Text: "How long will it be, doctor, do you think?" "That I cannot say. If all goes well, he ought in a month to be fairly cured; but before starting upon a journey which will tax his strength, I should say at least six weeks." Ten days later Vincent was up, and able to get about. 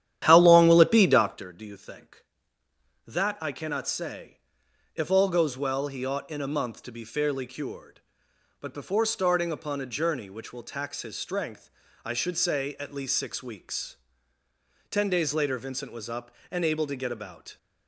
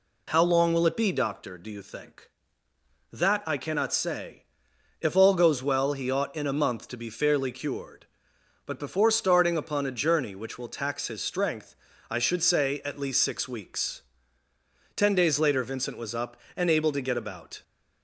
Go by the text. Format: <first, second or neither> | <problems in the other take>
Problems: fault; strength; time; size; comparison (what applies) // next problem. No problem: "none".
second | starts louder than the rest; strong; until 1.5 s; 11 dB